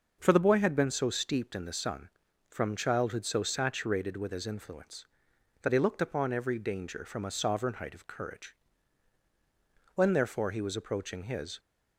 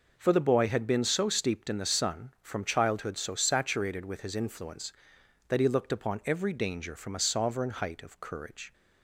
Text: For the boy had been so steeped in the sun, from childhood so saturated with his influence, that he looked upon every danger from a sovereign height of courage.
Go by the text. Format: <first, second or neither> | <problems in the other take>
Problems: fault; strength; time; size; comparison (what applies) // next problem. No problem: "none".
second | goes on to say "When therefore he was approaching his"; from 9.9 s on; 1.6 s long